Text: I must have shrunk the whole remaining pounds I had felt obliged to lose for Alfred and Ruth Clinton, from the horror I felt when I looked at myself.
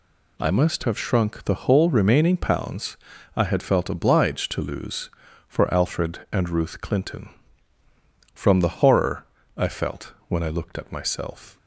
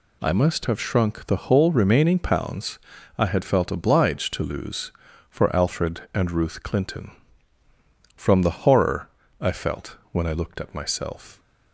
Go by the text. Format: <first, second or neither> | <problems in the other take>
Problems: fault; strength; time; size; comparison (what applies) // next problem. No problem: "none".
neither | pauses between "pounds" and "I"; the same in both // pauses between "horror" and "I"; slight; the same in both // pauses between "felt" and "when"; slight; the same in both